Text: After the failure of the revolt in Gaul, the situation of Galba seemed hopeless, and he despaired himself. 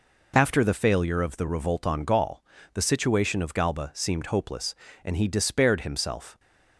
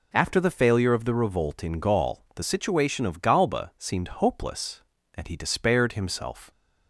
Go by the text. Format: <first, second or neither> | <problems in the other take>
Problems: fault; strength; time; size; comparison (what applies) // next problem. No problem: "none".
second | says "on" for "in"; at 1.8 s